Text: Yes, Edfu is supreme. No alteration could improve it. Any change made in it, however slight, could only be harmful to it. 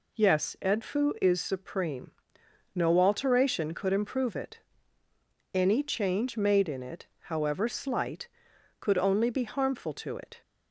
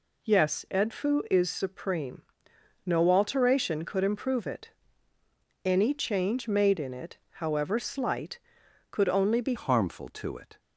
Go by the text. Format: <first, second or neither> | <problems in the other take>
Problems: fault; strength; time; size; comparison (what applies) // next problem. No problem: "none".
first | changes voice at "harmful"; from 9.5 s on; 1.0 s long